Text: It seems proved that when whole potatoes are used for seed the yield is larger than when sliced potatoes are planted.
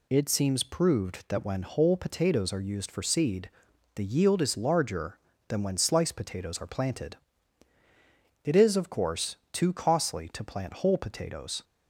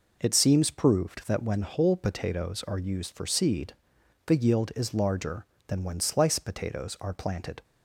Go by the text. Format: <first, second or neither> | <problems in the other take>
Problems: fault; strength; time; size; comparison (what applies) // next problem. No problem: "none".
second | pauses between "seed" and "the"; noticeable; at 3.4 s; 0.46 s long; noticeable in the second // goes on to say "It is of course too costly to plant whole potatoes"; strong; from 8.4 s on; 3.2 s long